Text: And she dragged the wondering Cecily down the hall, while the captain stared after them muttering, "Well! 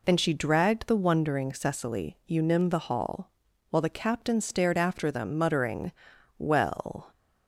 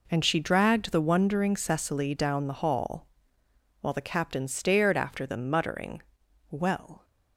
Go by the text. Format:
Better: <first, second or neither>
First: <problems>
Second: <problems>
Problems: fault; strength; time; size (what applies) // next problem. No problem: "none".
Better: second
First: says "unim" for "down"; at 2.2 s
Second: none